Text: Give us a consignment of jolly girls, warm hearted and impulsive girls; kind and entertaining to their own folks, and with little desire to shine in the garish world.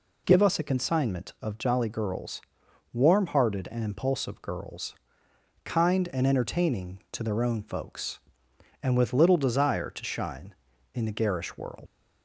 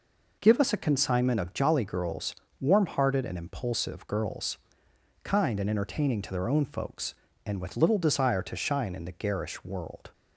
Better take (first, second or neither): second